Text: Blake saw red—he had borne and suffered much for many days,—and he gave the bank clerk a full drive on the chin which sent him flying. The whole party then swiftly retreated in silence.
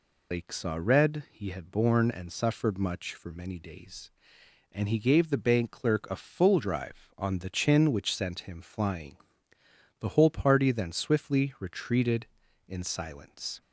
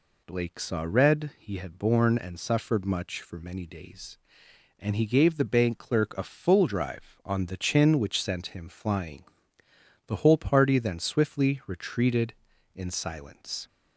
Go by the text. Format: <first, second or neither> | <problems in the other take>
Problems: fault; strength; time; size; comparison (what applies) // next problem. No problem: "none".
second | loses the start of "Blake"; at 0.3 s; 125 ms